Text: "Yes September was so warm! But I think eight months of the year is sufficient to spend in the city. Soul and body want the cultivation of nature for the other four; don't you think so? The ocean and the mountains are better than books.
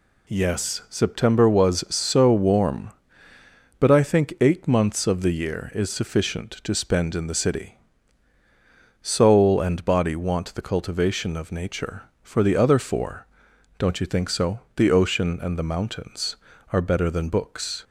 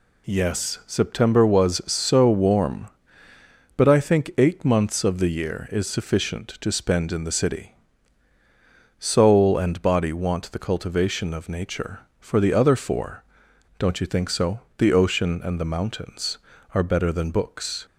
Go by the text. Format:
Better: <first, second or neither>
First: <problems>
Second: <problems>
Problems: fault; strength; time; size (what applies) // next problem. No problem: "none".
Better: neither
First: none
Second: none